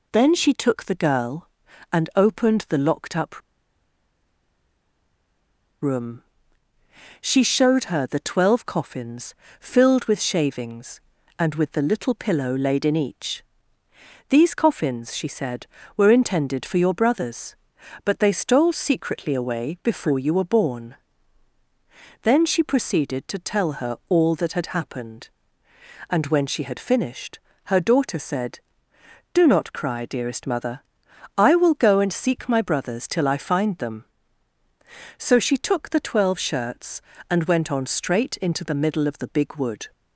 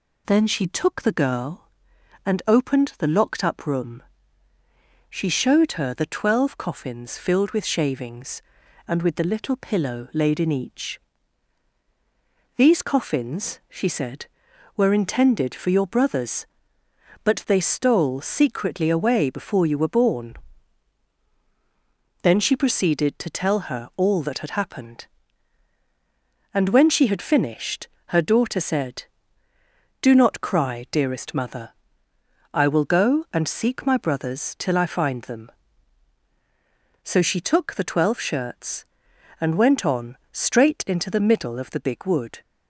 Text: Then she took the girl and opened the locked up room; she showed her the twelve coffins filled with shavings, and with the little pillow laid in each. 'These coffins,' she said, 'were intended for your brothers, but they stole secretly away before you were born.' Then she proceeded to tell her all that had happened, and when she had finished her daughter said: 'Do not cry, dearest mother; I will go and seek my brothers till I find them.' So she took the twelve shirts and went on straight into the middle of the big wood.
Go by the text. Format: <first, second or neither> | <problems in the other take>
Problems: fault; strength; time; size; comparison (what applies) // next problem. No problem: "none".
second | pauses between "up" and "room"; strong; at 3.4 s; 2.4 s long // pauses between "coffins" and "filled"; slight; at 9.3 s; 0.28 s long // pauses between "finished" and "her"; slight; at 27.3 s; 0.26 s long; slight in the second